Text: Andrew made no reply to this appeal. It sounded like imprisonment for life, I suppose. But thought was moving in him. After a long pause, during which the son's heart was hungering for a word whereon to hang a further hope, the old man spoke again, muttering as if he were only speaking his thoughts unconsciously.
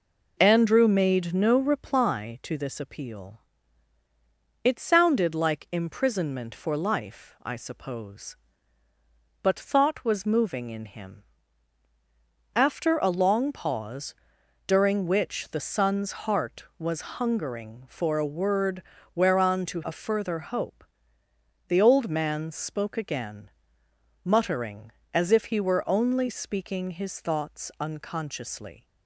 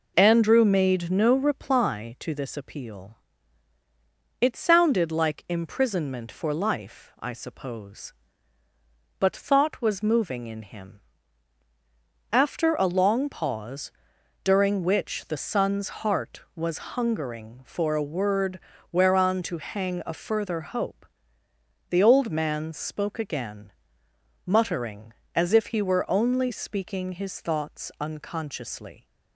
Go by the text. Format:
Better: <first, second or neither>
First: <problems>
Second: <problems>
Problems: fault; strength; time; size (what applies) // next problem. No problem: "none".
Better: second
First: pauses between "word" and "whereon"; slight; at 18.8 s; 0.32 s long // skips "hang"; at 19.8 s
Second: pauses between "word" and "whereon"; slight; at 18.6 s; 0.32 s long